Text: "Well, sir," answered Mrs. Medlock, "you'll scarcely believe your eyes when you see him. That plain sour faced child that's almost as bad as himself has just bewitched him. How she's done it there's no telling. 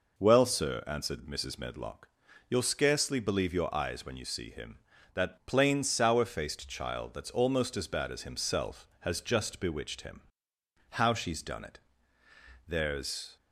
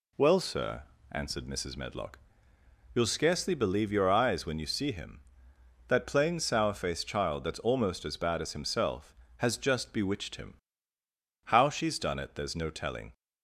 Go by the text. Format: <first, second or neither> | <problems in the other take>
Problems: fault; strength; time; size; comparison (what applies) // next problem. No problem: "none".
second | pauses between "it" and "there's"; noticeable; at 11.8 s; 0.86 s long // stops before "no telling"; at 13.3 s